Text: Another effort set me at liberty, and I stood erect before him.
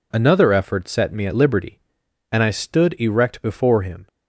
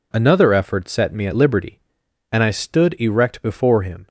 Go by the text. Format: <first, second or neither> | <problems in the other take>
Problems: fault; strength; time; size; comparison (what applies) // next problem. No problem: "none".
neither | none